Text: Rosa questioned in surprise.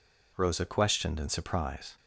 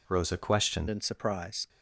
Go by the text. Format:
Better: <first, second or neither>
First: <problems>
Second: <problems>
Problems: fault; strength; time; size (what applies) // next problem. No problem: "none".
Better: first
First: none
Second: changes voice at "in"; from 0.8 s on; 0.8 s long